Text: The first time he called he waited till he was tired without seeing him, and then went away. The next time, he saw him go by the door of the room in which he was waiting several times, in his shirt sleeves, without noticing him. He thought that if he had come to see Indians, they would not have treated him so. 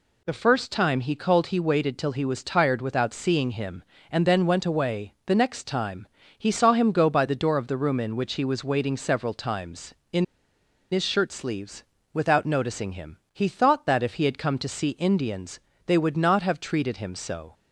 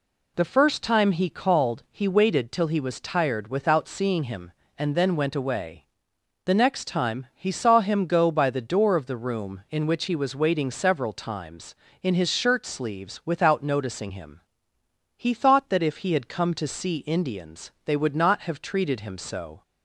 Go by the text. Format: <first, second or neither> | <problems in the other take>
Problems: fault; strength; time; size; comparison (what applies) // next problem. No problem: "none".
second | pauses between "in" and "his"; noticeable; at 10.2 s; 0.66 s long